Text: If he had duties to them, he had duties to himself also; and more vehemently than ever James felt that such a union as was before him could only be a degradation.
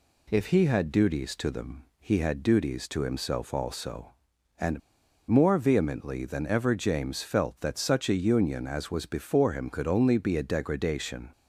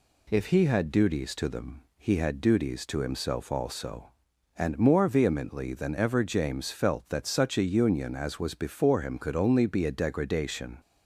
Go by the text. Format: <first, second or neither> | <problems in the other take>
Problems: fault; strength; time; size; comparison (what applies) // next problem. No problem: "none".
second | pauses between "and" and "more"; noticeable; at 4.7 s; 0.49 s long